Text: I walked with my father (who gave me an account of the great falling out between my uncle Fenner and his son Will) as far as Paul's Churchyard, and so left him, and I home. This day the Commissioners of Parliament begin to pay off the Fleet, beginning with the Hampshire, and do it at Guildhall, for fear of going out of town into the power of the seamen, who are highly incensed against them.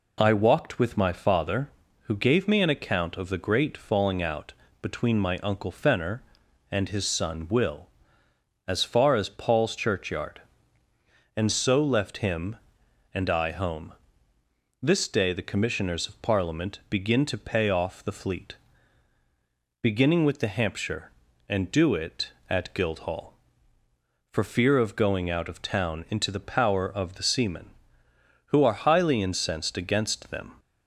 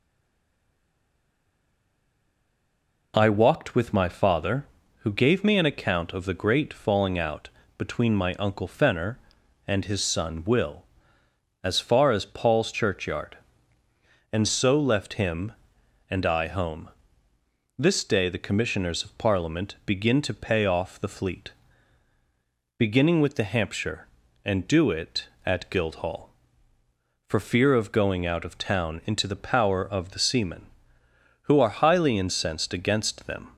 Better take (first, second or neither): first